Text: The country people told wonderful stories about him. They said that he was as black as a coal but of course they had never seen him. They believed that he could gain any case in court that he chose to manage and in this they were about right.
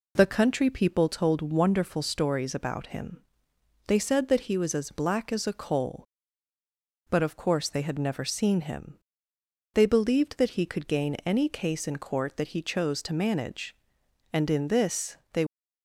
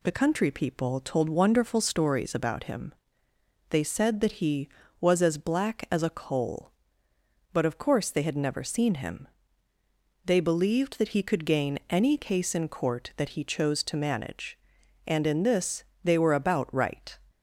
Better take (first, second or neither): second